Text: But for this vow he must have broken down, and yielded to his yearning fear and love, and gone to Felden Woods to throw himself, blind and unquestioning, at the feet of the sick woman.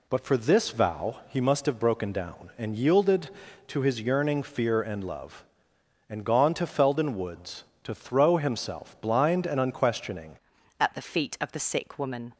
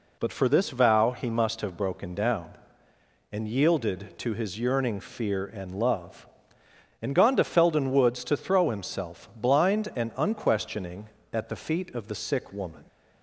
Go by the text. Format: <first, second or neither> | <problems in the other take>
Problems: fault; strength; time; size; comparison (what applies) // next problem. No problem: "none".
second | changes voice at "at"; from 10.7 s on; 1.6 s long